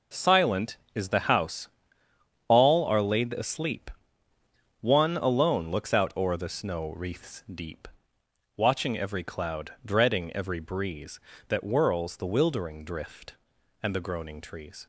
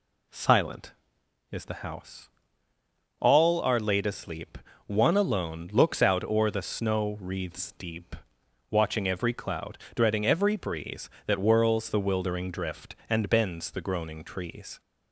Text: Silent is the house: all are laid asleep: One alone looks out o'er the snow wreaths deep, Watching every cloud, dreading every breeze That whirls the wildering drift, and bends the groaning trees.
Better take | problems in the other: second | skips "bends"; at 13.9 s

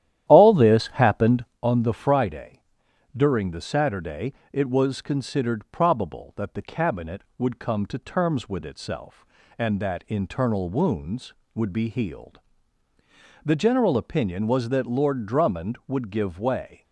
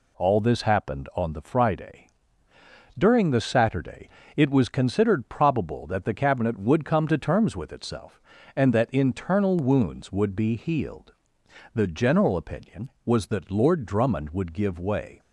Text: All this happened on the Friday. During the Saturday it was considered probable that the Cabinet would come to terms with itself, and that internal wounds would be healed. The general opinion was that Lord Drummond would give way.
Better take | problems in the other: second | starts louder than the rest; strong; until 1.6 s; 12 dB // pauses between "Saturday" and "it"; slight; at 4.3 s; 0.18 s long; slight in the second

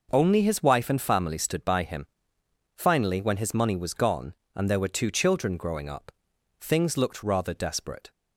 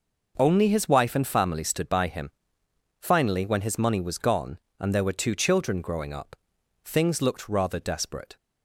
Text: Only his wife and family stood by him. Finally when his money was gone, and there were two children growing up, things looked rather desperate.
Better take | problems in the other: neither | none

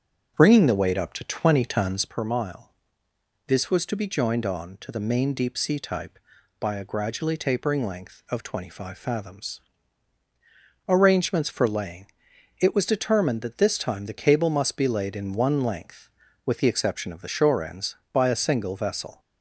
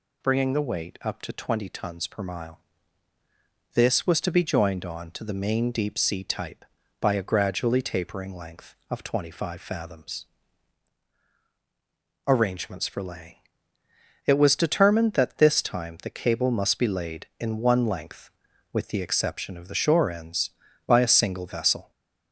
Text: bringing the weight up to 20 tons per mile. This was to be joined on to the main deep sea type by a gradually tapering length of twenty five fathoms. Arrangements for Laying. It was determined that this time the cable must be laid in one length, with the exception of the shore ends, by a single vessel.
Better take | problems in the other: second | starts louder than the rest; strong; until 2.2 s; 7.5 dB

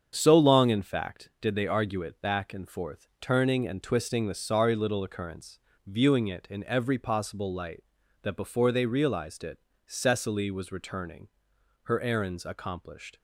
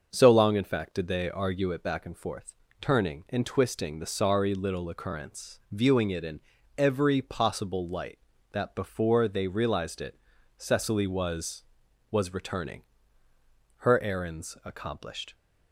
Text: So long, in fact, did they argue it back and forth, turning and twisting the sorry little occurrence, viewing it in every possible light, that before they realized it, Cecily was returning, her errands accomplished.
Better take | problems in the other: first | starts louder than the rest; until 1.1 s; 6 dB; strong in the first // pauses between "in" and "every"; slight; at 6.4 s; 0.36 s long // says "was" twice; at 12.1 s

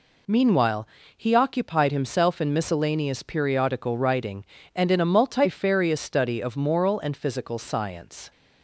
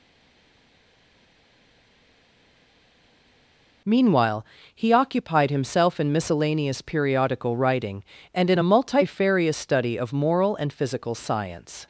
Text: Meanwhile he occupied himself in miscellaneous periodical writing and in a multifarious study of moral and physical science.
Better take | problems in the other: first | stays silent before the first word; strong; until 3.8 s; 3.8 s long // pauses between "Meanwhile" and "he"; slight; at 4.4 s; 0.28 s long; slight in the first

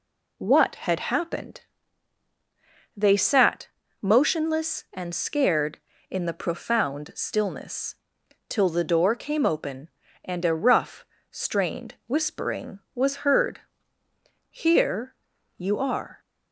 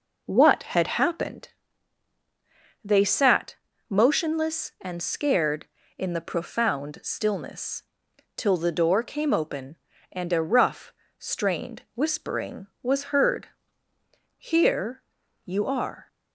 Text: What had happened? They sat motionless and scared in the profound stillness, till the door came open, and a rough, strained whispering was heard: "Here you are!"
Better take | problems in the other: first | starts louder than the rest; noticeable; until 1.5 s; 5 dB // pauses between "sat" and "motionless"; slight; at 3.5 s; 0.34 s long; slight in the first // pauses between "Here" and "you"; at 15.0 s; 0.44 s long; also in the first

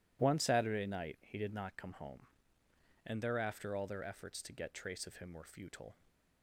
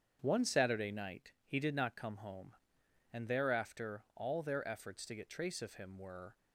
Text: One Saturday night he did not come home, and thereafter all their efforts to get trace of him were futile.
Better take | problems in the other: first | starts louder than the rest; strong; until 1.2 s; 8 dB // stops before "futile"; at 6.3 s

